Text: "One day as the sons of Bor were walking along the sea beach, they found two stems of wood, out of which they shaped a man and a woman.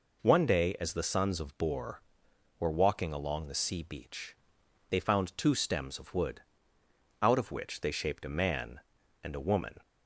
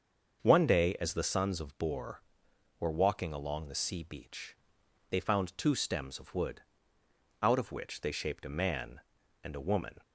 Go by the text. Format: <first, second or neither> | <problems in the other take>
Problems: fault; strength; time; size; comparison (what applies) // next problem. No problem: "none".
first | starts louder than the rest; until 1.4 s; 6.5 dB